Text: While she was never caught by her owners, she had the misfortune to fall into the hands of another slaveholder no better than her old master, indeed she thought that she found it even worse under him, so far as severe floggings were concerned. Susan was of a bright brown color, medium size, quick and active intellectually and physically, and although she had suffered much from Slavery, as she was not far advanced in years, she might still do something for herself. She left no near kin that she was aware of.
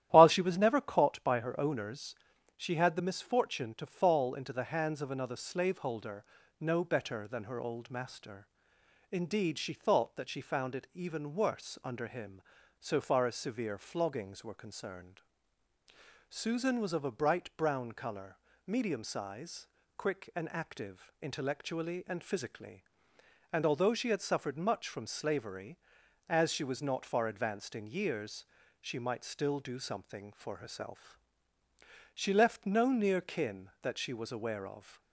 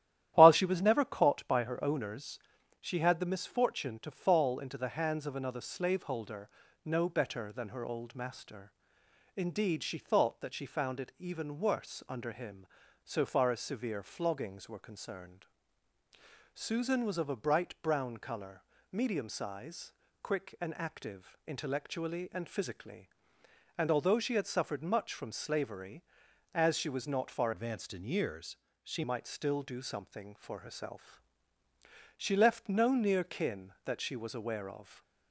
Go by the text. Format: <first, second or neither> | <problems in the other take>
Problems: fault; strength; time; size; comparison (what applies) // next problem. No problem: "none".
first | starts louder than the rest; strong; until 1.3 s; 12 dB; strong in the first // pauses between "slaveholder" and "no"; slight; at 6.4 s; 0.36 s long; slight in the first // changes voice from "advanced" to "she"; from 27.5 to 29.0 s; 1.5 s long